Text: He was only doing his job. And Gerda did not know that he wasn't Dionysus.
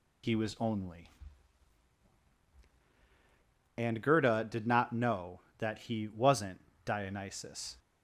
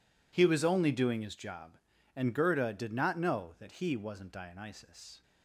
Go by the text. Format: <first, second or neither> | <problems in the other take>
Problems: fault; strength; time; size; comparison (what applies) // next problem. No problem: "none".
second | skips "doing his job"; at 2.4 s // pauses between "wasn't" and "Dionysus"; slight; at 6.6 s; 0.26 s long